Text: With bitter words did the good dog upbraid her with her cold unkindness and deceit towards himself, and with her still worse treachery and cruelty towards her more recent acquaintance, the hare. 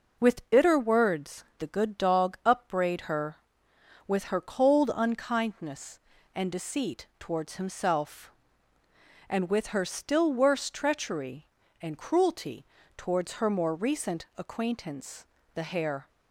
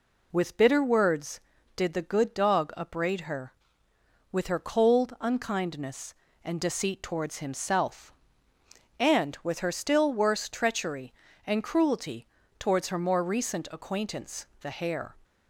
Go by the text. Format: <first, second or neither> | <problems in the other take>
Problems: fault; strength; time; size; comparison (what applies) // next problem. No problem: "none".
second | skips "did"; at 1.5 s // pauses between "cruelty" and "towards"; slight; at 12.6 s; 0.32 s long; slight in the second